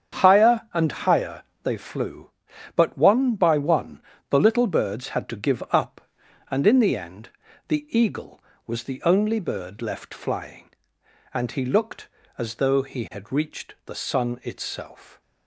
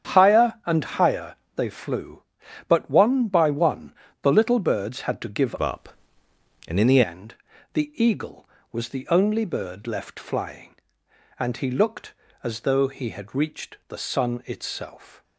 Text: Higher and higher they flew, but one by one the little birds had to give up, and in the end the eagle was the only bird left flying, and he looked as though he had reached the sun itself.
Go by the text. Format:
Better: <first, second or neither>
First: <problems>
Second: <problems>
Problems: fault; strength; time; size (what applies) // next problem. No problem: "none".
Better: first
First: starts louder than the rest; strong; until 1.2 s; 8 dB // pauses between "higher" and "they"; slight; at 1.4 s; 0.22 s long // pauses between "one" and "the"; slight; at 3.9 s; 0.30 s long // pauses between "end" and "the"; at 7.2 s; 0.38 s long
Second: starts louder than the rest; strong; until 1.1 s; 8.5 dB // pauses between "higher" and "they"; slight; at 1.3 s; 0.22 s long // pauses between "one" and "the"; slight; at 3.9 s; 0.30 s long // changes voice from "up" to "the"; from 5.6 to 7.0 s; 1.4 s long // pauses between "end" and "the"; at 7.3 s; 0.38 s long